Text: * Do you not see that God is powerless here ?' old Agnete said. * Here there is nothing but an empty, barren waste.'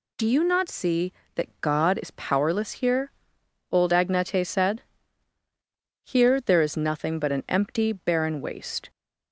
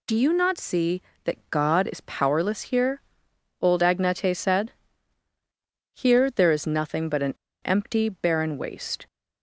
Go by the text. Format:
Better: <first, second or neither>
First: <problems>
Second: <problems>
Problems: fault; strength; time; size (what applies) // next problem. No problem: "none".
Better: first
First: none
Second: pauses between "an" and "empty"; slight; at 7.3 s; 0.29 s long